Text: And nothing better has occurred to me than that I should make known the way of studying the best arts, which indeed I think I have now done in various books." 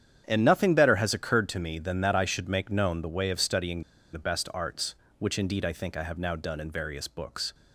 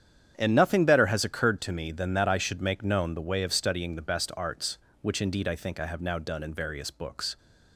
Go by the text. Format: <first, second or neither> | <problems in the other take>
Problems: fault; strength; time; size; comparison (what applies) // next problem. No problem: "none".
second | starts louder than the rest; strong; until 1.2 s; 9 dB; strong in the second // pauses between "studying" and "the"; slight; at 3.8 s; 0.31 s long